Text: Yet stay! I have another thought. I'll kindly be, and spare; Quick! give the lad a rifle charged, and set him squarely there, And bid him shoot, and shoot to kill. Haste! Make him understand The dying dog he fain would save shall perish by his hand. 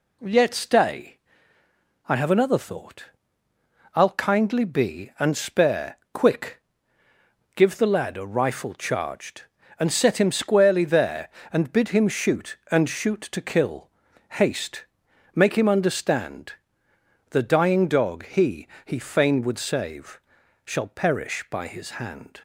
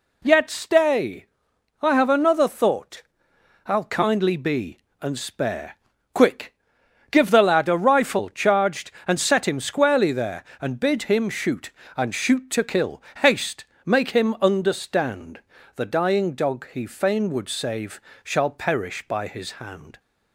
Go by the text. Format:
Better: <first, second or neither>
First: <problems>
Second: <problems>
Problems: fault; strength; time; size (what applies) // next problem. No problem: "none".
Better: second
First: pauses between "understand" and "The"; noticeable; at 16.5 s; 0.76 s long // says "he" twice; at 18.8 s // pauses between "save" and "shall"; noticeable; at 20.1 s; 0.46 s long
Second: pauses between "understand" and "The"; slight; at 15.4 s; 0.34 s long // pauses between "save" and "shall"; slight; at 17.9 s; 0.24 s long